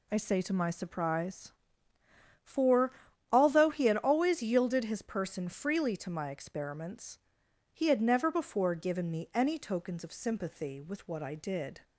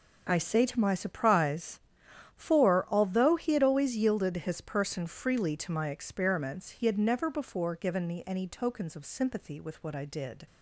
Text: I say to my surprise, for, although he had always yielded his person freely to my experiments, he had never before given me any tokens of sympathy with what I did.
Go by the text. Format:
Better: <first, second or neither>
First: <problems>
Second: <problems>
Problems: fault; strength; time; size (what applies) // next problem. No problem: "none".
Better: neither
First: none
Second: none